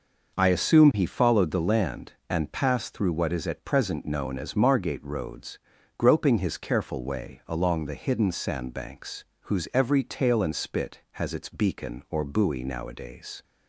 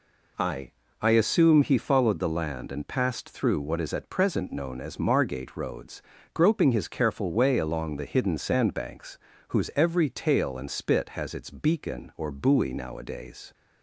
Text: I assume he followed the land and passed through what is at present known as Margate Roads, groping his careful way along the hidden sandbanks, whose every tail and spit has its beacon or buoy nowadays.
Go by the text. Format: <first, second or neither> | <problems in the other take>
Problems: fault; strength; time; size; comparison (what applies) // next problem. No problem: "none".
first | says "I" twice; at 1.0 s